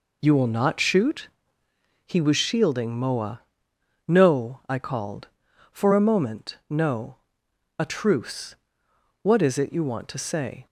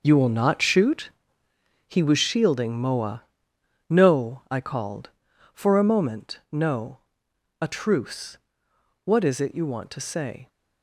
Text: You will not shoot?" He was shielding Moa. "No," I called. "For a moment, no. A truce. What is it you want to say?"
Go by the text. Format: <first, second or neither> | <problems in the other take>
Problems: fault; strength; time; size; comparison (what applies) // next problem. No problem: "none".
first | gets quieter; strong; throughout; 10 dB